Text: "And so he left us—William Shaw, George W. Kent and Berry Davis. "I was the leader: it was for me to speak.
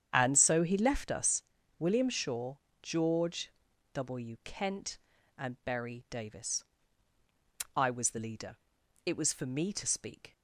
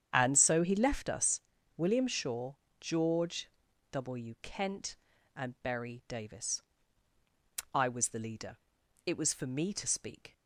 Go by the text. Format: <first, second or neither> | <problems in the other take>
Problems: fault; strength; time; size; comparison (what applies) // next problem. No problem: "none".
neither | starts louder than the rest; strong; the same in both // pauses between "George" and "W"; the same in both